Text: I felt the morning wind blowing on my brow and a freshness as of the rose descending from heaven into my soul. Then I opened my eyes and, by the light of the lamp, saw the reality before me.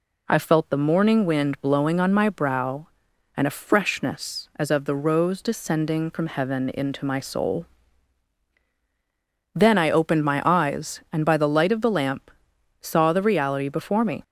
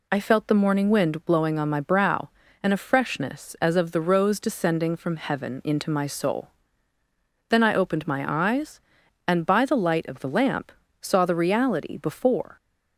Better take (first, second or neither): first